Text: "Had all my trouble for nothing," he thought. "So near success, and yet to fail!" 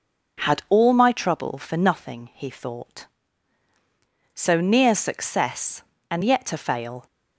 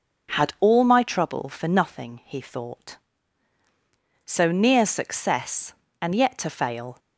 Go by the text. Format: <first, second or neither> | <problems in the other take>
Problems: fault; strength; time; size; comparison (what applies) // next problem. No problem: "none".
neither | none